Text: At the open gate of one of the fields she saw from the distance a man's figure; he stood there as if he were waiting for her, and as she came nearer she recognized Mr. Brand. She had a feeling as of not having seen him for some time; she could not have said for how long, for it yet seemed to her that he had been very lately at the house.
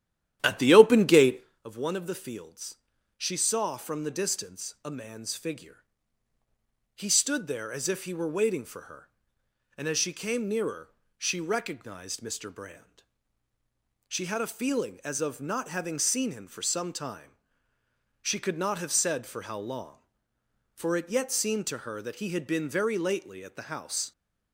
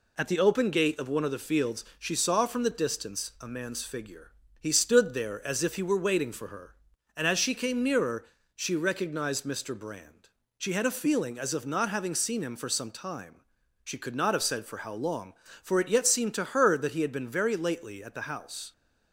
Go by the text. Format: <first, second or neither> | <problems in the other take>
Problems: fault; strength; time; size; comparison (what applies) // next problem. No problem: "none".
second | starts louder than the rest; strong; until 1.5 s; 11.5 dB // pauses between "fields" and "she"; at 2.7 s; 0.40 s long // pauses between "nearer" and "she"; slight; at 10.9 s; 0.26 s long; slight in the second